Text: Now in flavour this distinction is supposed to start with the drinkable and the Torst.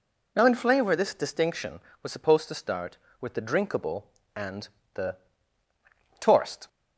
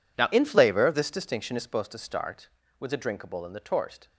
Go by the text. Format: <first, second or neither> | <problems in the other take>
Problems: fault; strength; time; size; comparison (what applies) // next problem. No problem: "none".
second | says "was" for "is"; at 2.0 s // pauses between "and" and "the"; slight; at 4.6 s; 0.26 s long // pauses between "the" and "Torst"; at 5.1 s; 1.0 s long